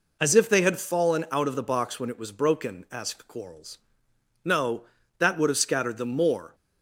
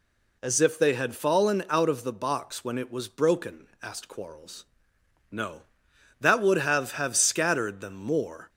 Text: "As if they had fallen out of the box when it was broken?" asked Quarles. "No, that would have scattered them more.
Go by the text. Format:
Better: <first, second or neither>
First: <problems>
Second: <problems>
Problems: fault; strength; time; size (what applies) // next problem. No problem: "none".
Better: first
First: none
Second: says "have" twice; at 6.9 s